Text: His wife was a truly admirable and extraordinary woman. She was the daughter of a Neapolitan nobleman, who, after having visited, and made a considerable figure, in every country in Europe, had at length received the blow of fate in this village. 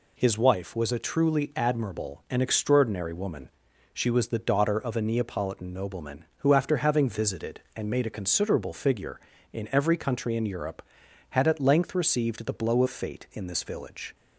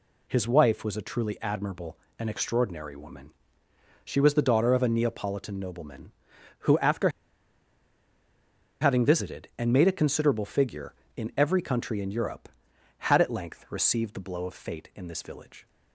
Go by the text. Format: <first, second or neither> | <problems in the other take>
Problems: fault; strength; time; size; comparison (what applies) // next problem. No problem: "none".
first | pauses between "after" and "having"; strong; at 7.0 s; 1.7 s long